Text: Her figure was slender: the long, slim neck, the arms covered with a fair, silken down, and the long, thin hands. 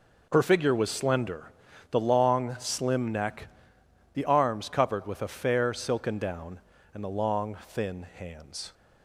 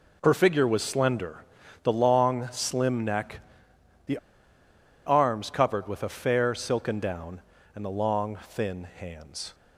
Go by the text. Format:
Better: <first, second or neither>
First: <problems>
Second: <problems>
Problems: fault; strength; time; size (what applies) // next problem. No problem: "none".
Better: first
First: none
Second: pauses between "the" and "arms"; noticeable; at 4.1 s; 0.88 s long